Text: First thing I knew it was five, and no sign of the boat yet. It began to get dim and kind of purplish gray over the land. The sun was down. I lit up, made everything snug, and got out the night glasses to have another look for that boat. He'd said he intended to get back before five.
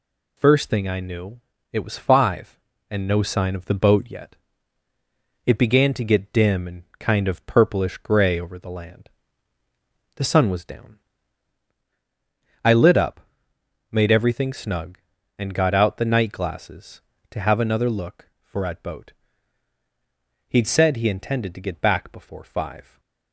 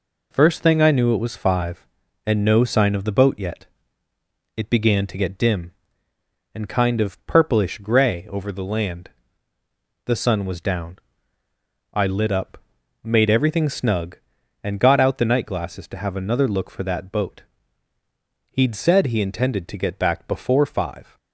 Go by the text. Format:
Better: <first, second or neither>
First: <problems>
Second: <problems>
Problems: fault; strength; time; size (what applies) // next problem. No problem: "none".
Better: second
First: pauses between "knew" and "it"; slight; at 1.3 s; 0.32 s long // pauses between "and" and "kind"; slight; at 6.8 s; 0.16 s long // says "at" for "that"; at 18.6 s // stays silent after the last word; slight; from 22.8 s on; 0.5 s long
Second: none